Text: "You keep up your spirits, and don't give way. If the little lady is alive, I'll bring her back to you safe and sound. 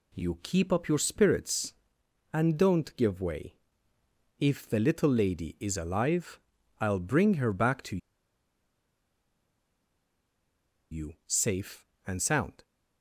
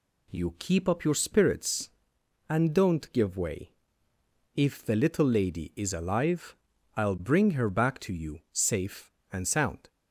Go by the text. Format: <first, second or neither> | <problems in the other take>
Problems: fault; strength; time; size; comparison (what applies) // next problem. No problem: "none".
second | pauses between "to" and "you"; strong; at 7.9 s; 2.9 s long